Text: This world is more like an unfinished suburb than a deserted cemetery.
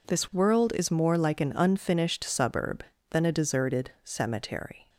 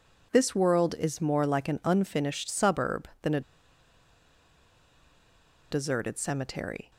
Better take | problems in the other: first | pauses between "a" and "deserted"; strong; at 3.4 s; 2.3 s long

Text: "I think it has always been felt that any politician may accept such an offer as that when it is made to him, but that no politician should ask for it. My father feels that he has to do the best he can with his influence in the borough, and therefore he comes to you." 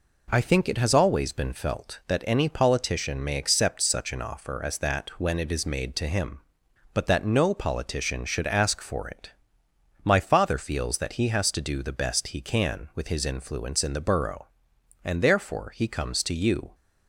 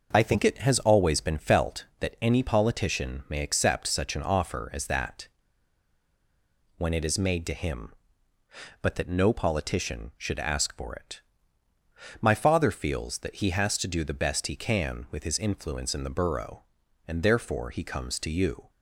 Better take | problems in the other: first | pauses between "that" and "when"; strong; at 5.2 s; 1.4 s long

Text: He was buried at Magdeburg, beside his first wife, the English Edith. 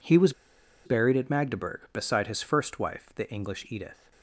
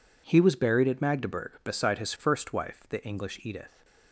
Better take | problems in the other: second | pauses between "was" and "buried"; noticeable; at 0.3 s; 0.52 s long

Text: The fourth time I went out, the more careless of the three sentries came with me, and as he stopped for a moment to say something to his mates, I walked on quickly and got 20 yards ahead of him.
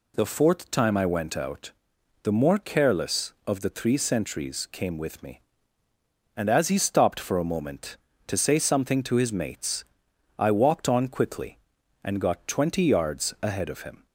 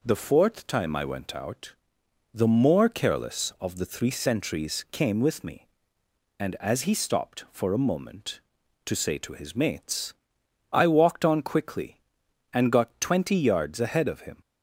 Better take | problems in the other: first | skips "something"; at 9.1 s

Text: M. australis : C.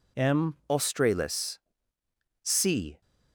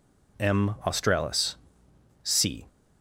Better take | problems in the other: second | changes voice at "australis"; from 0.6 s on; 2.4 s long

